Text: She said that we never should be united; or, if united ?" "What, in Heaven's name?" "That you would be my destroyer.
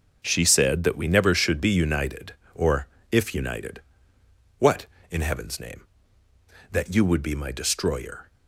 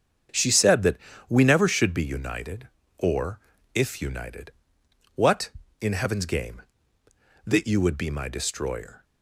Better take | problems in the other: first | starts louder than the rest; strong; until 1.6 s; 8 dB; also in the first // pauses between "that" and "we"; slight; at 0.9 s; 0.32 s long // says "game" for "name"; at 6.2 s

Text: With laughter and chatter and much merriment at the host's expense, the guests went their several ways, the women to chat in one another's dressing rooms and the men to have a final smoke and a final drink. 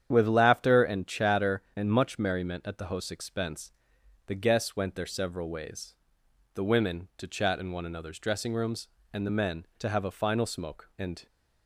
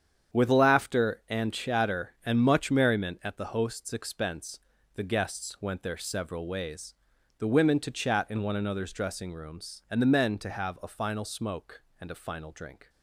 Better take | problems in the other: second | starts louder than the rest; strong; until 1.1 s; 9 dB; strong in the second // stops before "a final drink"; at 11.2 s

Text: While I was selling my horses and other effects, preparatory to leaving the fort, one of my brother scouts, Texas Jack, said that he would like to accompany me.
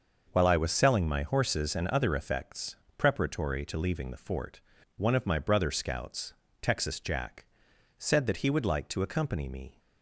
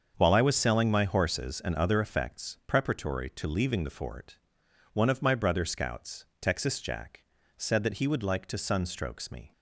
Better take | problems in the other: first | starts louder than the rest; until 1.1 s; 7 dB; noticeable in the first // says "sunstrokes" for "accompany"; at 8.5 s

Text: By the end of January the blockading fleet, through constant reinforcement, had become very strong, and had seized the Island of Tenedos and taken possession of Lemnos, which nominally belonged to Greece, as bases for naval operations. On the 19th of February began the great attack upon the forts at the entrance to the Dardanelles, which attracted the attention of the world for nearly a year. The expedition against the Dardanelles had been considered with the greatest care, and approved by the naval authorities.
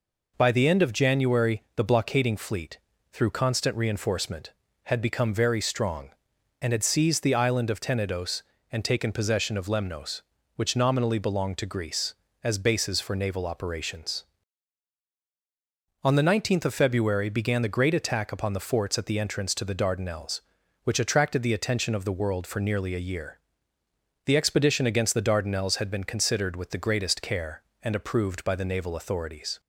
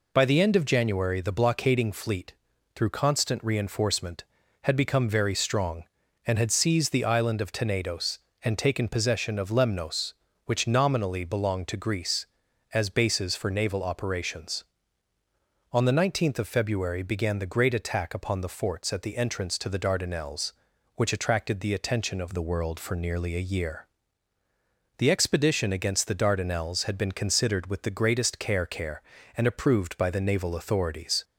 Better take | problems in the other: first | says "care" twice; at 28.6 s

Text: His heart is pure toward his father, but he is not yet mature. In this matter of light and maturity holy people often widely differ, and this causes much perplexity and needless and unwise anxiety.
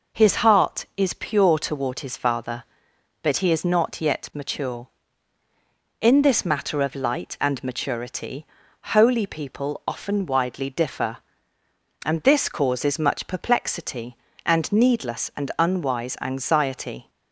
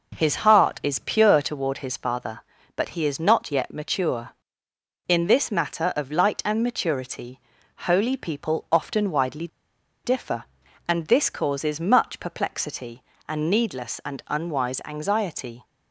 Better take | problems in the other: first | pauses between "maturity" and "holy"; noticeable; at 7.3 s; 0.50 s long; also in the first // pauses between "widely" and "differ"; noticeable; at 9.4 s; 0.57 s long

